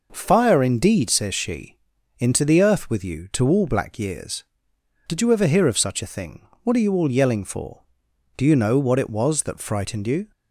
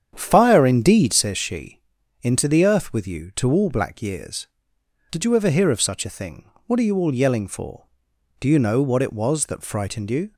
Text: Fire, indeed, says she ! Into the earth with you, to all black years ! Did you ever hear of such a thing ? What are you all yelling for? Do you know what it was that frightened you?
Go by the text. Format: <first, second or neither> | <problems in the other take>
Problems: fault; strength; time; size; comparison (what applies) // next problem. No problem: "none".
first | starts louder than the rest; strong; until 1.4 s; 8 dB